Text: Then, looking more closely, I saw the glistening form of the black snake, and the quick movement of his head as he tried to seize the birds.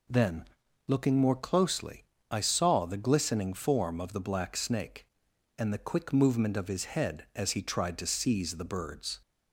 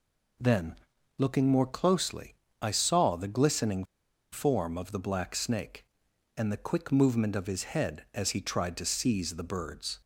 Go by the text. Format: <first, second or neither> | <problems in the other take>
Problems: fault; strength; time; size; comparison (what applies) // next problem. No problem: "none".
first | pauses between "glistening" and "form"; noticeable; at 3.8 s; 0.50 s long